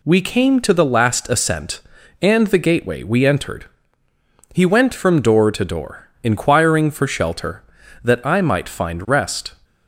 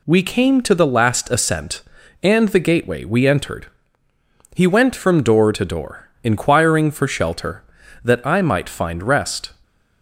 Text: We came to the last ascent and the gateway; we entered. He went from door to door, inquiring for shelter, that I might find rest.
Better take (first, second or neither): neither